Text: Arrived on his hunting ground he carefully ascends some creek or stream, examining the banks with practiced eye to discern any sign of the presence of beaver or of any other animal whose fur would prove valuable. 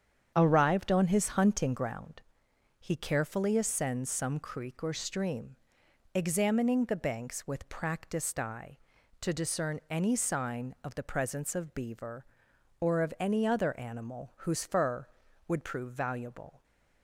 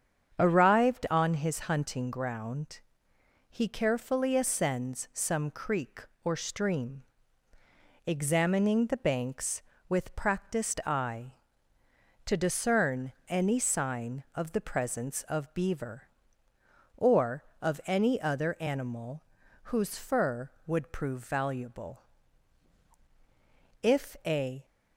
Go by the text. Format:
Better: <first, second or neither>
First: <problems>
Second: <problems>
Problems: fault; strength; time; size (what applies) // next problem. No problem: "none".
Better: first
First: starts louder than the rest; strong; until 1.3 s; 8 dB // pauses between "ground" and "he"; noticeable; at 2.2 s; 0.56 s long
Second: starts louder than the rest; strong; until 1.4 s; 8 dB // pauses between "ground" and "he"; noticeable; at 2.7 s; 0.72 s long // pauses between "discern" and "any"; slight; at 13.1 s; 0.16 s long // pauses between "animal" and "whose"; at 19.2 s; 0.44 s long // goes on to say "If a"; noticeable; from 23.8 s on; 0.82 s long